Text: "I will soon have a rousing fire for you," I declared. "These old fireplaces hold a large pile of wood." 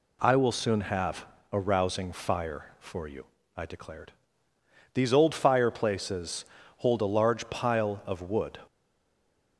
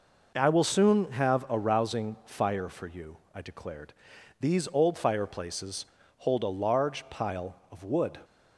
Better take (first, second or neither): second